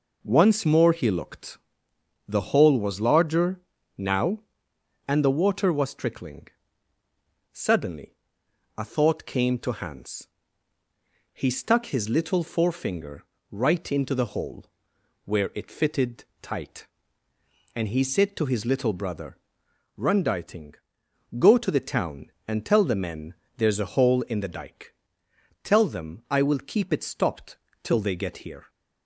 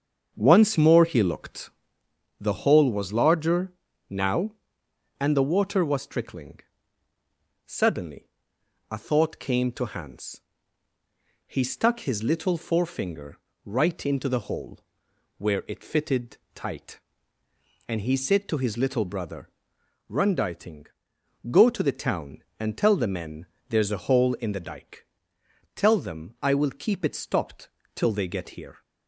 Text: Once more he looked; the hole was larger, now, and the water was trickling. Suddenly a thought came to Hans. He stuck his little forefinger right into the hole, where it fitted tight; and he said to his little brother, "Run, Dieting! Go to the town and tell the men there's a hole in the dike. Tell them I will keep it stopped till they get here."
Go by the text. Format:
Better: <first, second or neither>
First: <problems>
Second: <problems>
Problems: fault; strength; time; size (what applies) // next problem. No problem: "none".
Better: first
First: pauses between "Suddenly" and "a"; noticeable; at 8.1 s; 0.62 s long // pauses between "forefinger" and "right"; slight; at 13.2 s; 0.26 s long // pauses between "fitted" and "tight"; slight; at 16.2 s; 0.16 s long // pauses between "men" and "there's"; slight; at 23.3 s; 0.20 s long // pauses between "stopped" and "till"; slight; at 27.5 s; 0.28 s long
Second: starts louder than the rest; strong; until 2.2 s; 7 dB // pauses between "Suddenly" and "a"; noticeable; at 8.2 s; 0.62 s long // pauses between "forefinger" and "right"; slight; at 13.3 s; 0.26 s long // pauses between "fitted" and "tight"; slight; at 16.3 s; 0.16 s long // pauses between "men" and "there's"; slight; at 23.4 s; 0.20 s long // pauses between "stopped" and "till"; slight; at 27.6 s; 0.28 s long